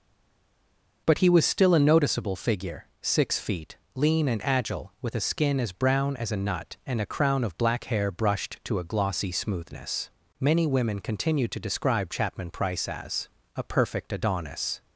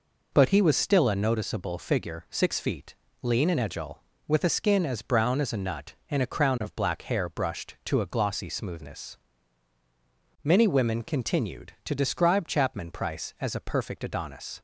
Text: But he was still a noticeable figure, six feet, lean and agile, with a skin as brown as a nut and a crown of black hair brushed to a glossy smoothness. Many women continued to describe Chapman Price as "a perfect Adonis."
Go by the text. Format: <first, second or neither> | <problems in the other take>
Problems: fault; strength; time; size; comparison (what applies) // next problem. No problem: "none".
second | stays silent before the first word; until 1.0 s; 1.0 s long // pauses between "as" and "a"; slight; at 13.2 s; 0.26 s long